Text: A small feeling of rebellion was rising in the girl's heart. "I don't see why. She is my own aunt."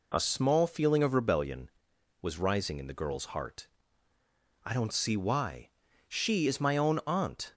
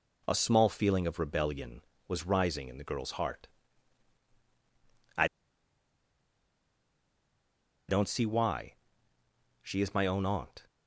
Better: first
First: none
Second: pauses between "I" and "don't"; strong; at 5.2 s; 2.6 s long

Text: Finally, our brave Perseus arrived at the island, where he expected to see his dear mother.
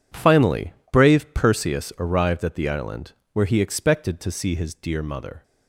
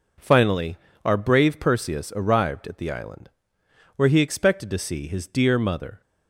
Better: second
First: skips "our"; at 0.8 s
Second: none

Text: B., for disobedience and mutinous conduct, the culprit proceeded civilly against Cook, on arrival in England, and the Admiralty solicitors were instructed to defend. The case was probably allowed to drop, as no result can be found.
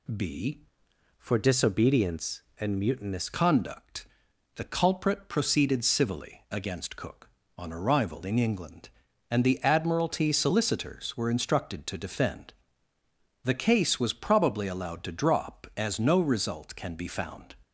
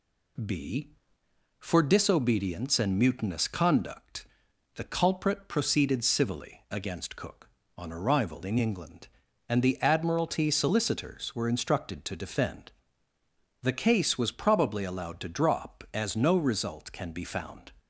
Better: second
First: changes voice from "for" to "mutinous"; from 1.1 to 3.2 s; 2.1 s long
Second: none

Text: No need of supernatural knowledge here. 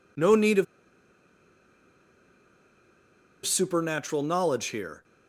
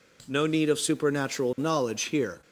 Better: second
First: pauses between "of" and "supernatural"; strong; at 0.6 s; 2.8 s long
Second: none

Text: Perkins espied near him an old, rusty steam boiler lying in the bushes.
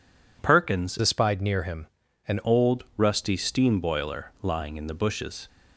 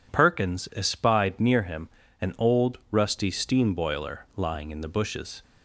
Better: second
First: changes voice from "espied" to "an"; from 0.9 to 2.3 s; 1.4 s long // pauses between "him" and "an"; at 1.8 s; 0.40 s long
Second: pauses between "him" and "an"; slight; at 1.8 s; 0.32 s long

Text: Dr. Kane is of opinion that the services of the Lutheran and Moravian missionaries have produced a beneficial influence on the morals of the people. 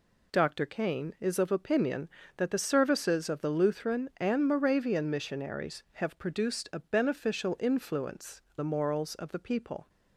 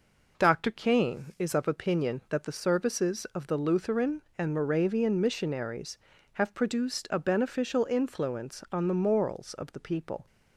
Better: second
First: skips "on"; at 8.5 s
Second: none

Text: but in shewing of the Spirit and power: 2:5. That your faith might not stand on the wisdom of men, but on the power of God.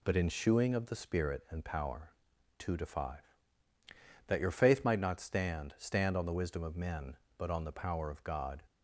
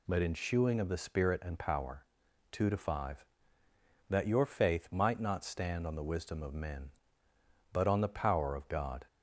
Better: second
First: says "stand" twice; at 5.7 s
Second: none

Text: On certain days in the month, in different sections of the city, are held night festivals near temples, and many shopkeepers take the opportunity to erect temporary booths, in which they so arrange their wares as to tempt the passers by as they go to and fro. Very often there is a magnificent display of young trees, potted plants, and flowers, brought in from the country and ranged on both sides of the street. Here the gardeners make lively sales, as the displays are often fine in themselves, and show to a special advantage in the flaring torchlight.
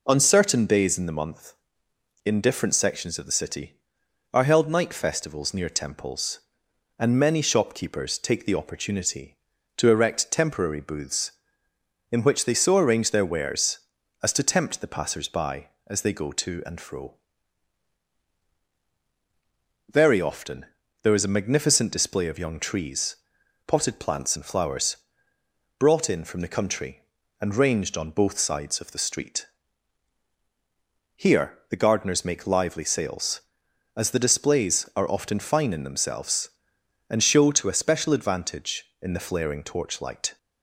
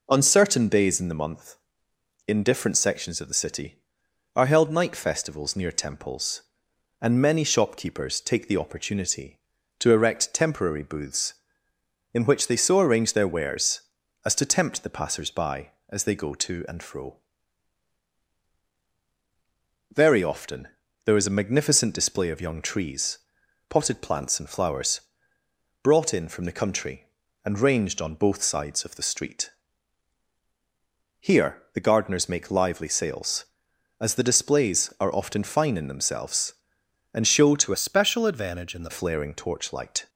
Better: first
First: pauses between "often" and "there"; slight; at 20.6 s; 0.36 s long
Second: pauses between "often" and "there"; slight; at 20.6 s; 0.36 s long // changes voice from "special" to "the"; from 37.7 to 38.8 s; 1.1 s long

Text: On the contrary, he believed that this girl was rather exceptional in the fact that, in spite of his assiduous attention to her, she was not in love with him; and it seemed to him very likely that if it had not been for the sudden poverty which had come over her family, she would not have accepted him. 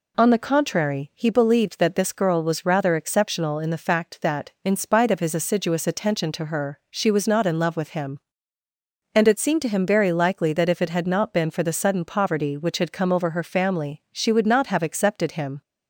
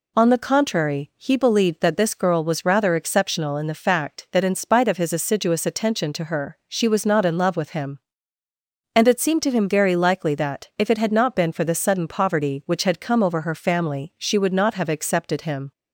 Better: neither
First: none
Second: none

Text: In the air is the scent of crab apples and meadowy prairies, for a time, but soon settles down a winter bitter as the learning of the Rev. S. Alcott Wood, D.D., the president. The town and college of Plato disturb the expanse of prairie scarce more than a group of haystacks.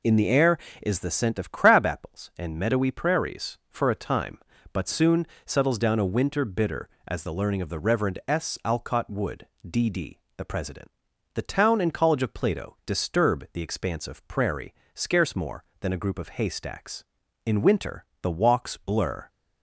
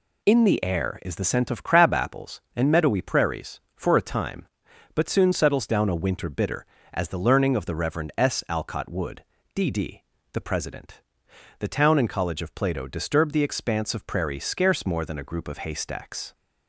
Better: second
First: pauses between "soon" and "settles"; slight; at 5.2 s; 0.20 s long // pauses between "prairie" and "scarce"; slight; at 14.7 s; 0.20 s long // goes on to say "In winter the walks blur"; strong; from 17.4 s on; 1.8 s long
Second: none

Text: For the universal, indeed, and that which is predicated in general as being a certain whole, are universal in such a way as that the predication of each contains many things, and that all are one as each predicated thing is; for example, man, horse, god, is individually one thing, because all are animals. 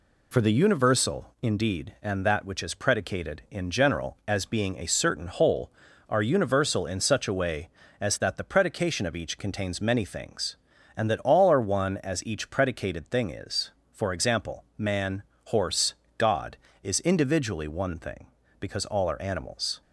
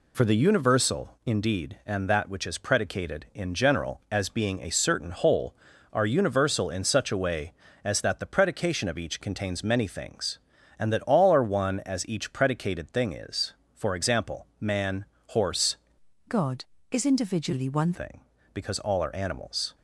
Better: first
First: none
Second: changes voice from "god" to "one"; from 16.2 to 17.9 s; 1.7 s long

